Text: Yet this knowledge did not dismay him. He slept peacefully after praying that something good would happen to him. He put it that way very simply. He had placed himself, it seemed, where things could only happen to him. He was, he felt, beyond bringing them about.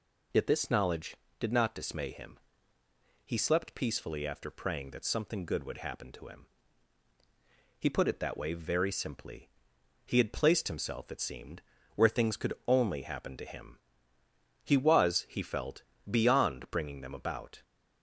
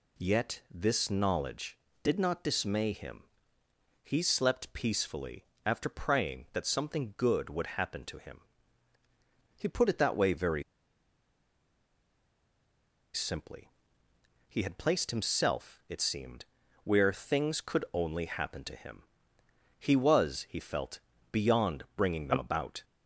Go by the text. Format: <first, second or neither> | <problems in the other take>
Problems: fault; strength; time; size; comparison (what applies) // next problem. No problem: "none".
first | pauses between "peacefully" and "after"; slight; at 5.4 s; 0.20 s long // pauses between "very" and "simply"; strong; at 10.6 s; 2.5 s long